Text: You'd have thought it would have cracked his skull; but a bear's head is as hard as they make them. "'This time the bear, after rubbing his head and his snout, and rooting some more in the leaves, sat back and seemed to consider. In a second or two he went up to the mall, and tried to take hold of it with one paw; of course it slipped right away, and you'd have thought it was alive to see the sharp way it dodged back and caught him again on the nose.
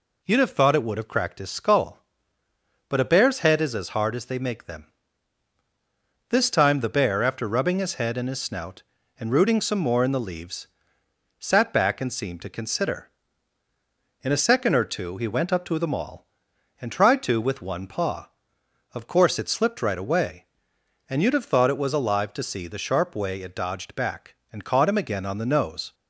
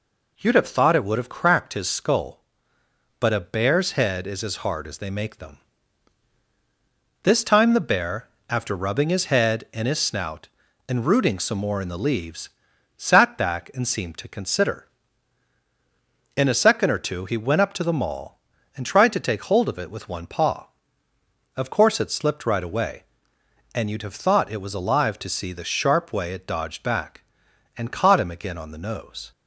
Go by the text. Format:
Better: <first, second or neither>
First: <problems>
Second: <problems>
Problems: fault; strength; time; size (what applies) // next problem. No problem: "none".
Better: second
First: skips "take hold of it"; at 17.3 s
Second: none